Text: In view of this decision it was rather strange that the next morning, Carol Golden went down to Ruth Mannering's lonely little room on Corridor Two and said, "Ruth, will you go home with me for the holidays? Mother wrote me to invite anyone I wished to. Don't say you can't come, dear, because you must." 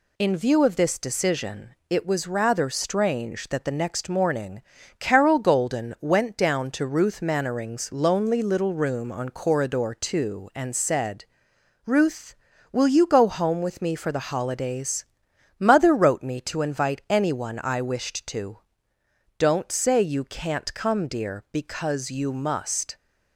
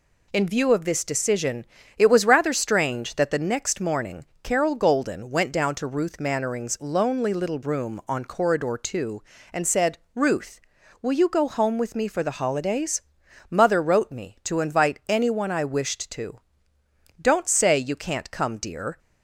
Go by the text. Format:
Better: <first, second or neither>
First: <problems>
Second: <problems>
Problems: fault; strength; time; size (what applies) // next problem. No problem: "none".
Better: first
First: none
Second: pauses between "decision" and "it"; slight; at 1.6 s; 0.32 s long // stops before "because you must"; at 18.9 s